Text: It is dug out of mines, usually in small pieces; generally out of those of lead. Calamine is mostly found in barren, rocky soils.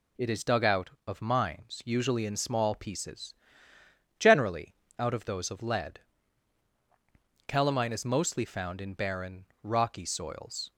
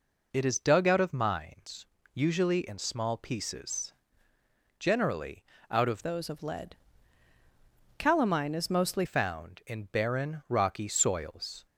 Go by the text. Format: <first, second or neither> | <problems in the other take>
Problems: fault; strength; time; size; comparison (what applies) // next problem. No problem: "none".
first | pauses between "generally" and "out"; slight; at 5.4 s; 0.26 s long; slight in the first // changes voice from "those" to "mostly"; from 6.0 to 9.0 s; 3.0 s long